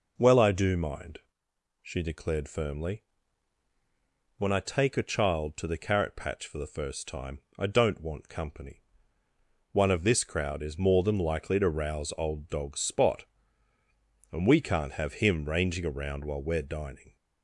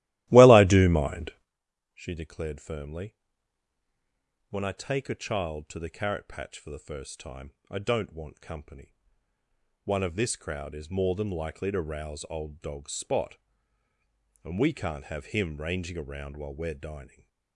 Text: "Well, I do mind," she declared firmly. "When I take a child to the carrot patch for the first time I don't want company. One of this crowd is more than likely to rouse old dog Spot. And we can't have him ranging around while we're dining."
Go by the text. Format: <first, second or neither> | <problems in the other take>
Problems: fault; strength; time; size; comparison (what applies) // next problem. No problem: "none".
first | starts louder than the rest; strong; until 1.6 s; 16 dB // pauses between "time" and "I"; slight; at 7.5 s; 0.16 s long; slight in the first